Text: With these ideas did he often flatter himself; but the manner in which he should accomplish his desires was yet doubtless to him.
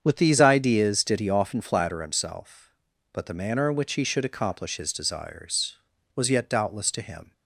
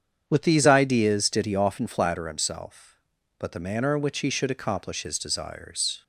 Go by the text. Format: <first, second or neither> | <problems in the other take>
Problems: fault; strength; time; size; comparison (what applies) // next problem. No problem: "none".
first | starts louder than the rest; strong; until 1.2 s; 8 dB; strong in the first // stops before "was yet doubtless to him"; at 6.0 s